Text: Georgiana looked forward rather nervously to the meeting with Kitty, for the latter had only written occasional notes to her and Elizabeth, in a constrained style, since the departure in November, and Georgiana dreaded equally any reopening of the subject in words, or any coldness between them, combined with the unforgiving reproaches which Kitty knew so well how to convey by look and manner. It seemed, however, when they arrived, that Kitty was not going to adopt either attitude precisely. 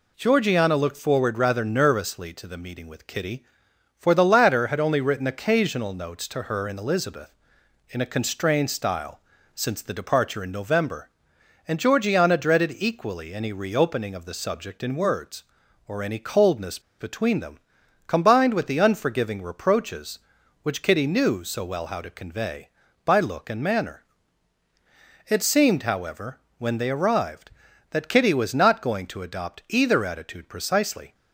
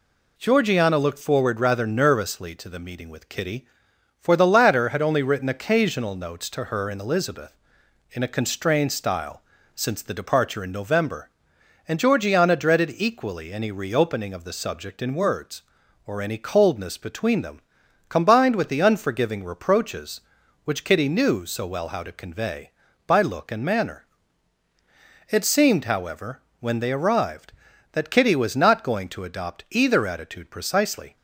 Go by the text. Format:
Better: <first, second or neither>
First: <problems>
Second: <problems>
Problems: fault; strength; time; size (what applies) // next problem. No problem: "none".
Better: second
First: pauses between "coldness" and "between"; slight; at 16.7 s; 0.20 s long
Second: none